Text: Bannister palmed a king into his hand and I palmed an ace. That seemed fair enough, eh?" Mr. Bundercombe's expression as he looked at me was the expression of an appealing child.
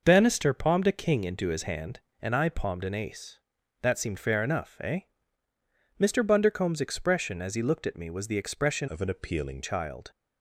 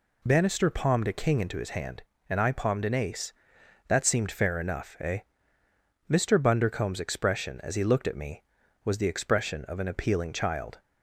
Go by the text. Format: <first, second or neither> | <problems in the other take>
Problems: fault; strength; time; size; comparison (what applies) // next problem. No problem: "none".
second | changes voice from "of" to "appealing"; from 8.8 to 9.6 s; 0.8 s long